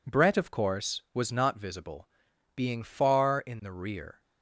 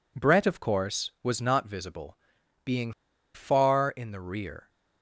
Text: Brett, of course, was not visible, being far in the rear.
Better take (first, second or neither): first